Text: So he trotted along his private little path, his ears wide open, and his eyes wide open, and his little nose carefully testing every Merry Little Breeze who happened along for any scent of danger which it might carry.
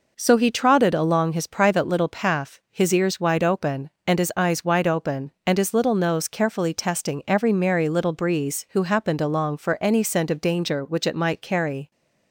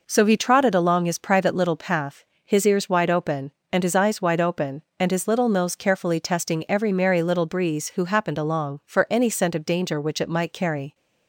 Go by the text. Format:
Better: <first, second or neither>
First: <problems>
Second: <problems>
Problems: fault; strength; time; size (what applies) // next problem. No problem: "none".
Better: neither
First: none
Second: none